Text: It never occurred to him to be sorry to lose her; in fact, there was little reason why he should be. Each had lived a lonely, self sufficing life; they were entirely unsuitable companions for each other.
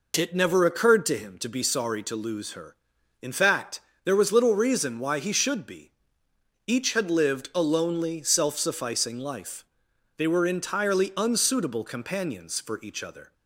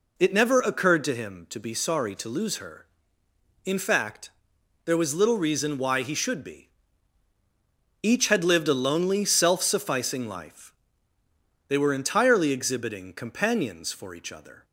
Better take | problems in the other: first | says "exhibiting" for "unsuitable"; at 12.5 s

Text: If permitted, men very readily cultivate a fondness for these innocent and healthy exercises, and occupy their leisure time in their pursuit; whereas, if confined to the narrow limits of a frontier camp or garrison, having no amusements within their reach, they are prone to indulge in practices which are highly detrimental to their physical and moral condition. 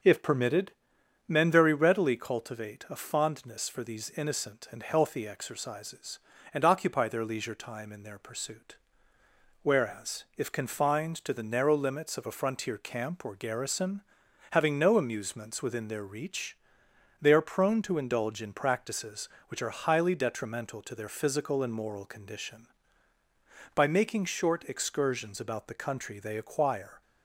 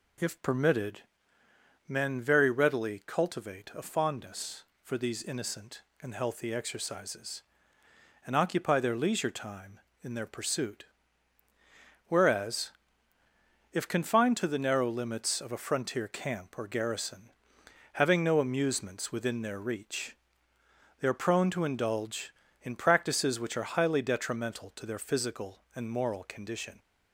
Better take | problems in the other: second | starts louder than the rest; until 1.6 s; 6 dB // goes on to say "By making short excursions about the country they acquire"; strong; from 23.7 s on; 3.2 s long

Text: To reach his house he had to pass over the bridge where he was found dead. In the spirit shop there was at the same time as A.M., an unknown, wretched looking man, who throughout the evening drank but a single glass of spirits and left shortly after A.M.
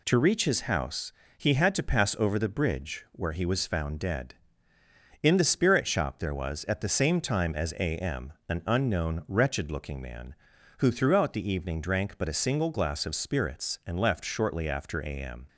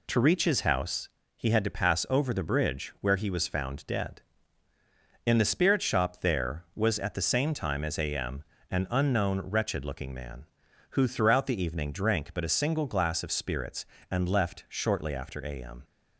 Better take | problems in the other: neither | pauses between "house" and "he"; slight; the same in both

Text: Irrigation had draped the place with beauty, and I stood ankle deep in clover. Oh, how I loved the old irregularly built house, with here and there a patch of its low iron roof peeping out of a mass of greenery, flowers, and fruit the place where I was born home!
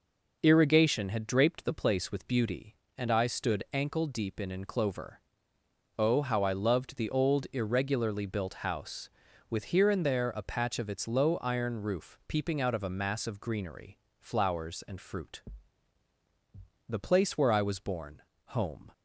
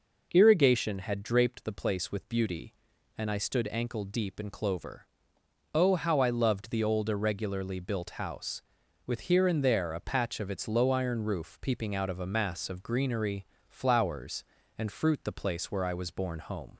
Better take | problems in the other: second | says "in" twice; at 4.5 s // pauses between "fruit" and "the"; strong; at 15.4 s; 1.4 s long // pauses between "born" and "home"; slight; at 18.2 s; 0.22 s long

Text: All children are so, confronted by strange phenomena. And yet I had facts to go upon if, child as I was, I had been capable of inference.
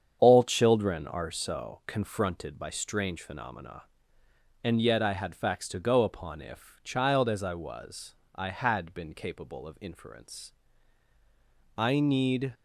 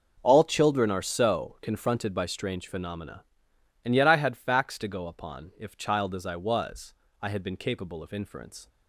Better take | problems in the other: second | starts louder than the rest; strong; until 1.2 s; 8 dB // goes on to say "I need"; noticeable; from 11.7 s on; 0.76 s long

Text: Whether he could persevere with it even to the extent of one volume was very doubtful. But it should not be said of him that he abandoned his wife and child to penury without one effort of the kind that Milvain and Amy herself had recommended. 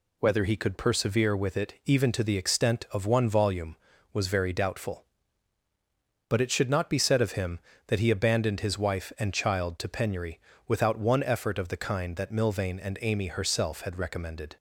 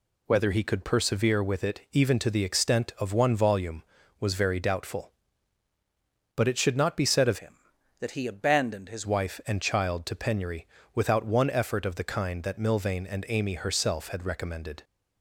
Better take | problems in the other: first | changes voice from "him" to "his"; from 7.3 to 9.0 s; 1.7 s long // pauses between "penury" and "without"; slight; at 10.6 s; 0.28 s long; slight in the first

